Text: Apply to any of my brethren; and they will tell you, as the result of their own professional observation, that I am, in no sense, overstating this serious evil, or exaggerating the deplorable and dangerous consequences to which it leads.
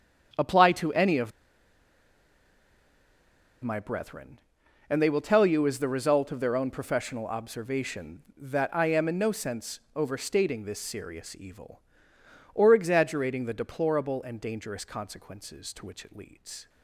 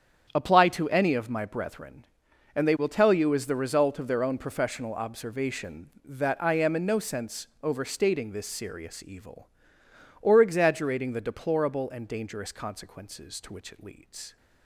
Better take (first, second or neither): second